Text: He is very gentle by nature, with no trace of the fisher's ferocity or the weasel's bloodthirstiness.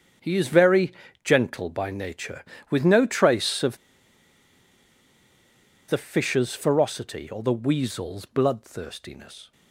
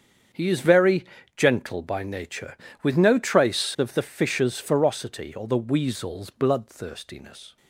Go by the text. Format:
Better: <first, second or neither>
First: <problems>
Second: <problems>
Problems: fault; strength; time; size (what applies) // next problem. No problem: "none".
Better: second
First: starts louder than the rest; strong; until 1.5 s; 7.5 dB // pauses between "very" and "gentle"; slight; at 0.9 s; 0.32 s long // pauses between "of" and "the"; strong; at 3.7 s; 2.1 s long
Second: starts louder than the rest; strong; until 1.6 s; 7.5 dB // pauses between "very" and "gentle"; slight; at 1.0 s; 0.32 s long